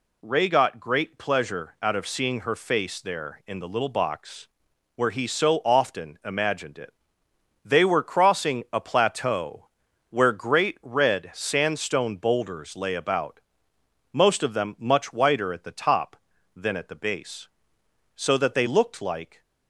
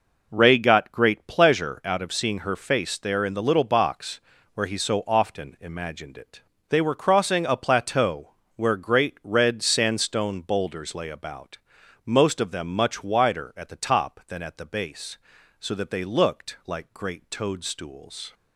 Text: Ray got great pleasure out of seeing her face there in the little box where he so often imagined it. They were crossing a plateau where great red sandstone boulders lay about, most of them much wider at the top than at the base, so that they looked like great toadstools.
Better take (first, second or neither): second